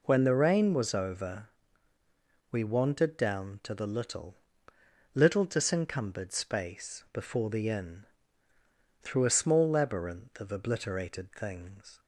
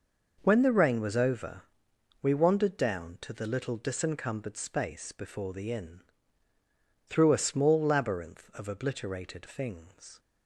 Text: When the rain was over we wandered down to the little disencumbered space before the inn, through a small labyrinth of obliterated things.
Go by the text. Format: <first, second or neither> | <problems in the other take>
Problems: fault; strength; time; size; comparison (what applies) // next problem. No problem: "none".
second | pauses between "over" and "we"; at 1.4 s; 1.0 s long; noticeable in the second // says "little" twice; at 5.1 s